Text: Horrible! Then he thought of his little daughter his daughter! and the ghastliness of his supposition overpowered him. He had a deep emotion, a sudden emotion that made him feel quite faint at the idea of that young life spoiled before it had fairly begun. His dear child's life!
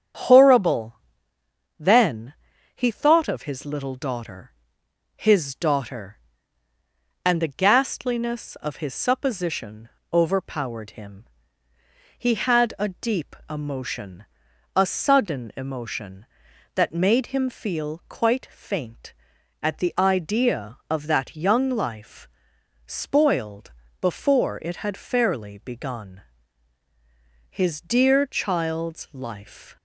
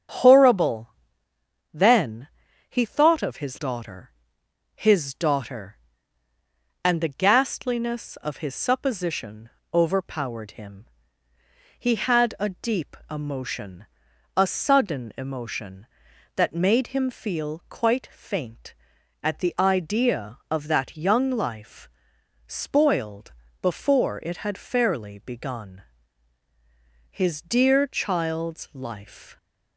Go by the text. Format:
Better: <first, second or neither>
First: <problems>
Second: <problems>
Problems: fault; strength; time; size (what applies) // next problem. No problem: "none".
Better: first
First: starts louder than the rest; strong; until 1.9 s; 8 dB // pauses between "Then" and "he"; at 2.3 s; 0.42 s long // pauses between "daughter" and "his"; noticeable; at 4.5 s; 0.62 s long // pauses between "supposition" and "overpowered"; slight; at 9.8 s; 0.24 s long // pauses between "deep" and "emotion"; slight; at 13.3 s; 0.16 s long // pauses between "life" and "spoiled"; noticeable; at 22.2 s; 0.58 s long // pauses between "spoiled" and "before"; slight; at 23.7 s; 0.28 s long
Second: starts louder than the rest; strong; until 1.9 s; 7.5 dB // pauses between "Then" and "he"; at 2.2 s; 0.42 s long // skips "little"; at 3.5 s // pauses between "daughter" and "his"; noticeable; at 4.1 s; 0.62 s long // pauses between "supposition" and "overpowered"; slight; at 9.4 s; 0.24 s long // pauses between "deep" and "emotion"; slight; at 12.9 s; 0.16 s long // pauses between "life" and "spoiled"; noticeable; at 21.8 s; 0.58 s long // pauses between "spoiled" and "before"; slight; at 23.3 s; 0.28 s long